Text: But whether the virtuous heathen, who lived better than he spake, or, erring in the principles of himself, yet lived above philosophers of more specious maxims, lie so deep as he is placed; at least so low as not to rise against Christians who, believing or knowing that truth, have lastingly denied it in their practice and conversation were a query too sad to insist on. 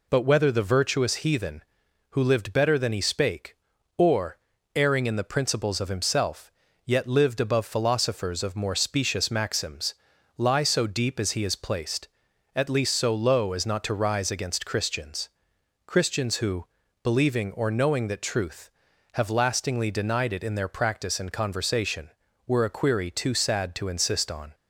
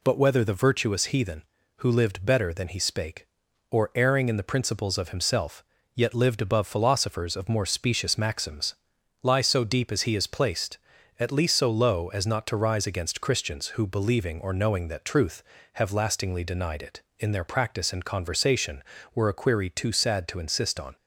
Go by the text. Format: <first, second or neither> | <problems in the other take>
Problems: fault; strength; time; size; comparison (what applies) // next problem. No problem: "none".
second | says "Christians" twice; at 15.8 s